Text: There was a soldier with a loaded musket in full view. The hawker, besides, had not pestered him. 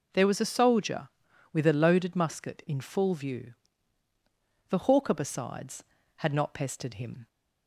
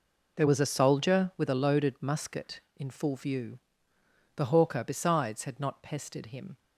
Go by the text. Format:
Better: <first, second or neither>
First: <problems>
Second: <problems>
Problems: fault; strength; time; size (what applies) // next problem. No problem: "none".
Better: neither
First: none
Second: none